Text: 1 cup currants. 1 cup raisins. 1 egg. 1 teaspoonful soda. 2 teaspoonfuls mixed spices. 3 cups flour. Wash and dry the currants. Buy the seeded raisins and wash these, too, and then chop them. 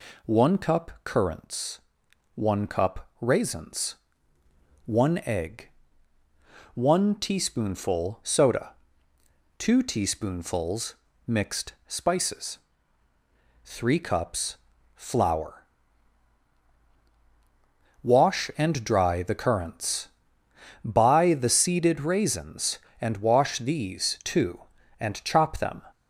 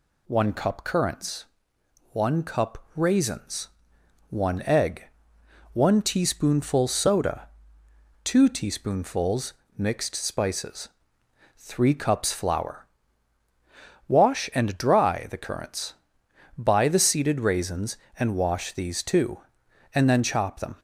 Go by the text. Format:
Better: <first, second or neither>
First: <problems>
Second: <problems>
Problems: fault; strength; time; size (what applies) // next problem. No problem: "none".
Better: second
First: pauses between "teaspoonfuls" and "mixed"; slight; at 10.9 s; 0.32 s long // pauses between "cups" and "flour"; at 14.5 s; 0.38 s long // skips "then"; at 25.2 s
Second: pauses between "teaspoonfuls" and "mixed"; slight; at 9.5 s; 0.24 s long